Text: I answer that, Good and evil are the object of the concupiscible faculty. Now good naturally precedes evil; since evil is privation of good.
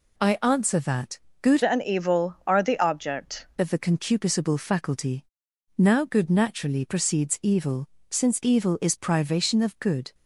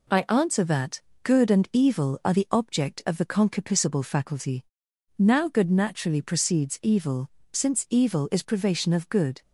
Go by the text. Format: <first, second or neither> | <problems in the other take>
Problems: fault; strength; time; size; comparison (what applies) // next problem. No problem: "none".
second | changes voice from "and" to "object"; from 1.6 to 3.4 s; 1.8 s long